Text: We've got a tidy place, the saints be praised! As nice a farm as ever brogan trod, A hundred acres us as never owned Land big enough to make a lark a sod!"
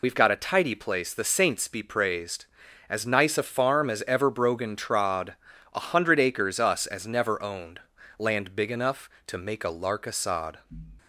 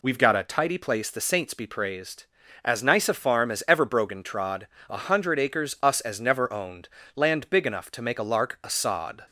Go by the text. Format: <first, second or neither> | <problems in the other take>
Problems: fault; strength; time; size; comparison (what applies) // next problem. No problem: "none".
second | loses the start of "We've"; at 0.0 s; 50 ms // pauses between "owned" and "Land"; at 7.7 s; 0.40 s long; slight in the second